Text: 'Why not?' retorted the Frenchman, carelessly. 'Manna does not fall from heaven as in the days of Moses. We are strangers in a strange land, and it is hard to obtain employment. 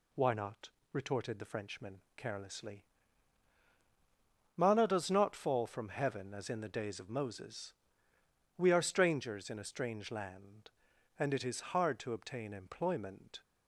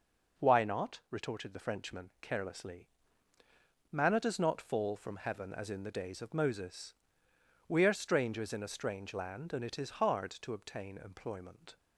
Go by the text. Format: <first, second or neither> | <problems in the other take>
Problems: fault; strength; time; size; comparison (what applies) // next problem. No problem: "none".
neither | none